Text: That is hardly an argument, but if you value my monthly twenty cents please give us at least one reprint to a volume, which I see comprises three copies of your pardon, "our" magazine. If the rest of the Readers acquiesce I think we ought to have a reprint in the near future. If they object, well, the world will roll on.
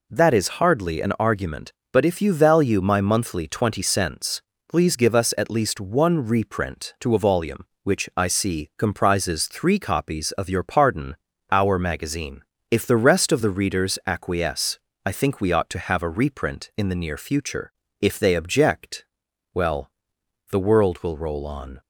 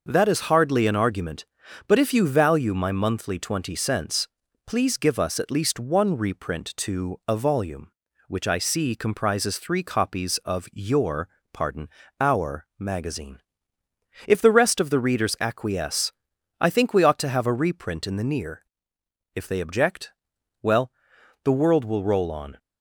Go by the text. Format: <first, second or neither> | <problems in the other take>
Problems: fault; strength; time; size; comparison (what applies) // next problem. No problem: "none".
first | pauses between "cents" and "please"; at 4.2 s; 0.40 s long; slight in the first // pauses between "your" and "pardon"; slight; at 11.2 s; 0.24 s long // pauses between "acquiesce" and "I"; noticeable; at 16.1 s; 0.48 s long; slight in the first // skips "future"; at 18.9 s